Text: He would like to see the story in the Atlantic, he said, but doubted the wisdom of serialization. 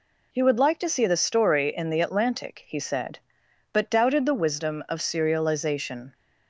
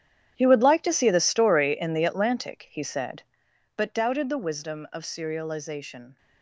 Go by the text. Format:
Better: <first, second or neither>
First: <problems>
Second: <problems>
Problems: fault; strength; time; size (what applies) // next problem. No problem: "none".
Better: first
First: none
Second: gets quieter; strong; throughout; 15 dB